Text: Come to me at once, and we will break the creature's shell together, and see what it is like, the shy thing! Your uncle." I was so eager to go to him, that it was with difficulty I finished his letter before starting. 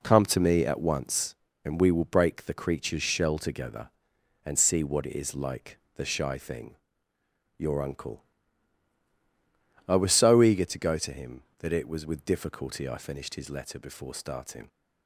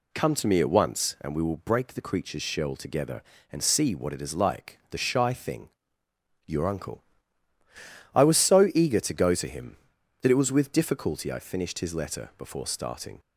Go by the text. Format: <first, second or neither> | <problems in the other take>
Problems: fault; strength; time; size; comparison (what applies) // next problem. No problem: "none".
neither | none